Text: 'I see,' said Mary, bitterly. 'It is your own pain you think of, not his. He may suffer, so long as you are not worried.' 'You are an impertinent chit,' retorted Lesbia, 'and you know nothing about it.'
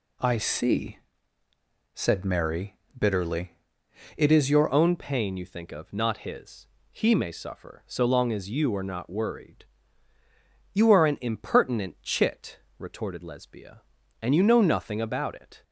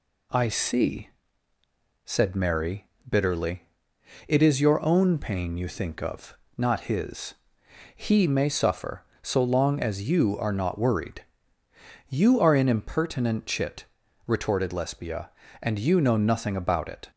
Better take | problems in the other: second | changes voice at "own"; from 4.7 s on; 10.9 s long

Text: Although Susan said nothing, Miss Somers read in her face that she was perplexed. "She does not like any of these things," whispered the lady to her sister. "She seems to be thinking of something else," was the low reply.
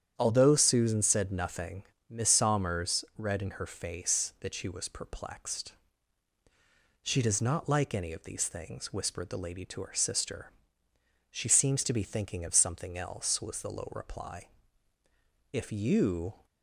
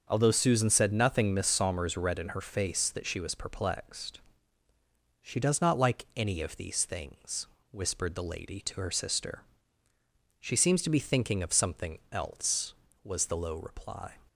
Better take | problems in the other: second | starts louder than the rest; strong; until 1.1 s; 9 dB; also in the second // goes on to say "If you"; noticeable; from 15.5 s on; 0.94 s long

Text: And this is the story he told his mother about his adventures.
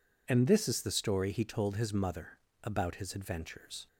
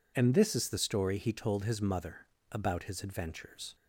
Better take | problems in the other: neither | pauses between "mother" and "about"; slight; the same in both

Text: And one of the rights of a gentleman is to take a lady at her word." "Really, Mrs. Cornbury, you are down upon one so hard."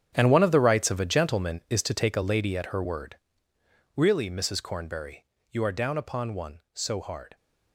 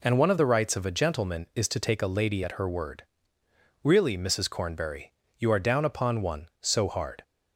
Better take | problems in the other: second | gets quieter; strong; throughout; 14.5 dB

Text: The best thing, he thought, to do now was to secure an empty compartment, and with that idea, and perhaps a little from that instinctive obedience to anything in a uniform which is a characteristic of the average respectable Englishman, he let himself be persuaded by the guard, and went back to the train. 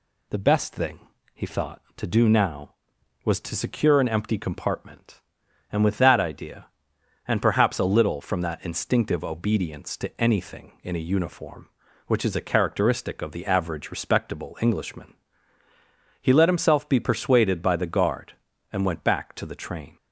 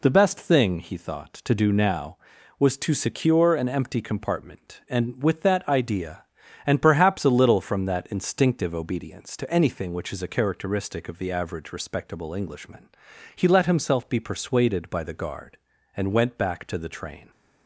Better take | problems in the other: first | skips "in a uniform"; at 9.9 s

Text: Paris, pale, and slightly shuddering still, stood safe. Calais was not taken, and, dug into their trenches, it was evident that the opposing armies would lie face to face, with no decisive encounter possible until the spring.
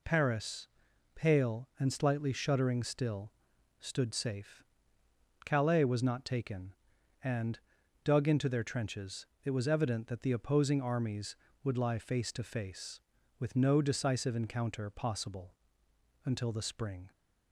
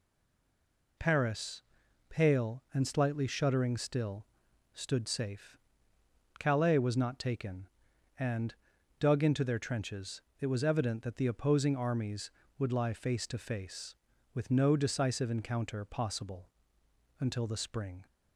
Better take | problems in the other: first | stays silent before the first word; until 0.9 s; 0.9 s long // pauses between "possible" and "until"; noticeable; at 16.4 s; 0.70 s long; noticeable in the first

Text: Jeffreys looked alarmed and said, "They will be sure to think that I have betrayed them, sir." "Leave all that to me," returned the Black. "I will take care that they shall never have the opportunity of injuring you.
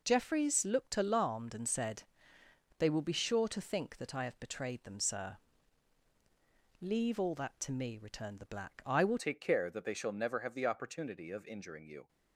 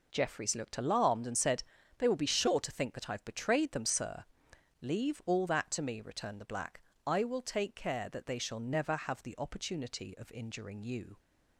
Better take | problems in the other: second | changes voice at "take"; from 9.1 s on; 2.9 s long

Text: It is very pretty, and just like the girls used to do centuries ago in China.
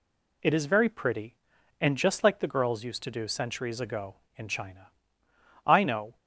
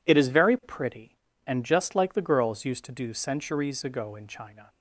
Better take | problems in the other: second | goes on to say "I know"; from 5.6 s on; 0.50 s long

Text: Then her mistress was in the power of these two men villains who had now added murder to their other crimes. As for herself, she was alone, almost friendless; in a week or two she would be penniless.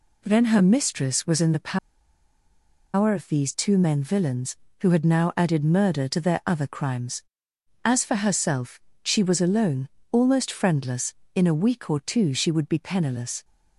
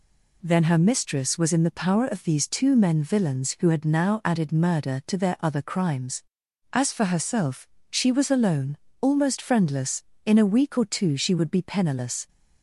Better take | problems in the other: second | pauses between "the" and "power"; at 1.7 s; 1.1 s long

